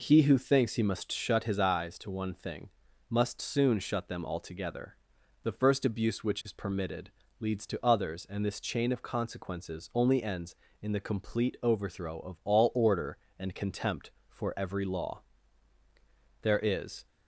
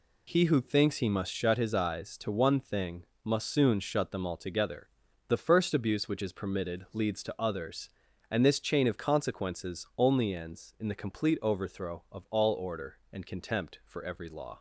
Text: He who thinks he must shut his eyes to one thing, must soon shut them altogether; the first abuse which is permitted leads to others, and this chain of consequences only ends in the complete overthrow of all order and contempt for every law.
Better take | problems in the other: second | pauses between "permitted" and "leads"; slight; at 7.1 s; 0.30 s long // goes on to say "There is"; noticeable; from 16.4 s on; 0.64 s long

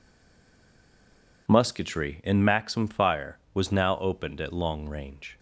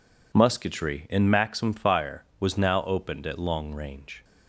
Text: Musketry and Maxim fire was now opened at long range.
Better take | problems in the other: second | stays silent before the first word; noticeable; until 1.4 s; 1.4 s long

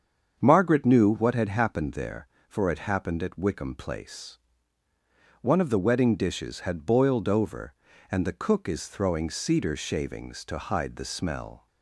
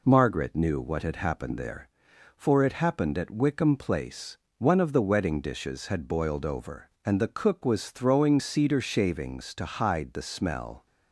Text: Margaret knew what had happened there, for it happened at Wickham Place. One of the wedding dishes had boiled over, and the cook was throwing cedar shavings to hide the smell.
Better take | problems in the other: second | starts louder than the rest; strong; until 1.4 s; 7 dB // says "is" for "was"; at 8.6 s

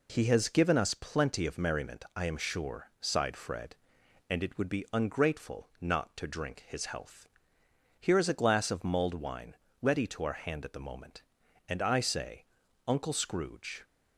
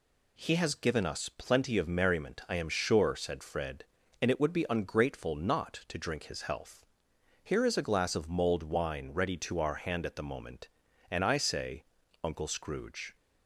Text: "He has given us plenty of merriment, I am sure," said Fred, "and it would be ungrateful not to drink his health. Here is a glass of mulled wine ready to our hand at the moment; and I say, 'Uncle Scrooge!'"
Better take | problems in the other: second | says "sighed" for "said"; at 2.9 s // pauses between "wine" and "ready"; slight; at 9.5 s; 0.26 s long

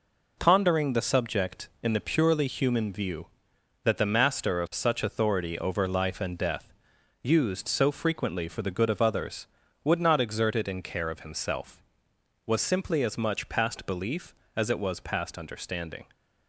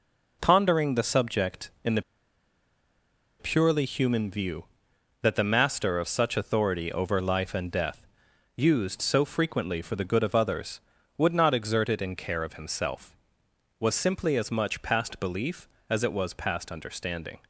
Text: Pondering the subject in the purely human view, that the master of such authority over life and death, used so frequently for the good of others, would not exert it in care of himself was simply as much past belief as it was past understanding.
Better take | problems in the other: first | pauses between "the" and "purely"; strong; at 2.0 s; 1.3 s long

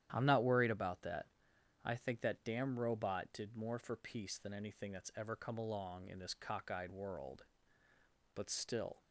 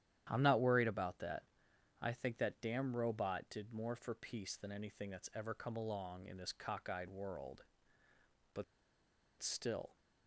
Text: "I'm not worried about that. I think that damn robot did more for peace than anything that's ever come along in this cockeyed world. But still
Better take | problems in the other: first | starts louder than the rest; strong; until 1.3 s; 11 dB; strong in the first // pauses between "But" and "still"; noticeable; at 8.6 s; 0.76 s long

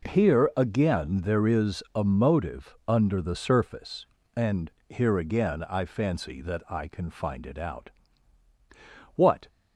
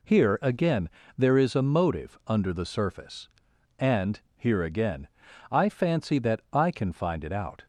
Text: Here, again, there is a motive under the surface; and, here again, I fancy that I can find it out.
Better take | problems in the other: second | goes on to say "What"; slight; from 9.1 s on; 0.32 s long

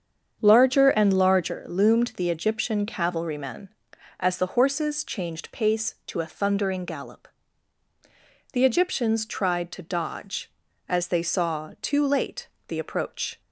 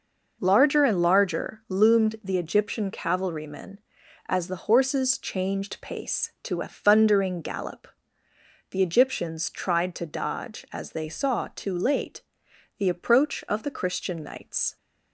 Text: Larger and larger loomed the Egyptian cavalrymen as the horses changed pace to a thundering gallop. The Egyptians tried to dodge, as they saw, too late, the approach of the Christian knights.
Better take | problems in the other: second | starts louder than the rest; strong; until 1.4 s; 7.5 dB // stops before "of the Christian knights"; at 13.4 s

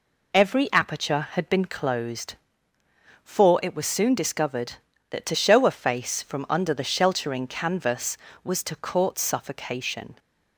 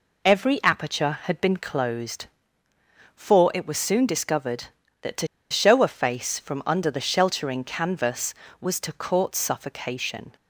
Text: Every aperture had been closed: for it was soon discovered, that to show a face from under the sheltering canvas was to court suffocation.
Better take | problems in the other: first | pauses between "to" and "show"; slight; at 5.2 s; 0.24 s long

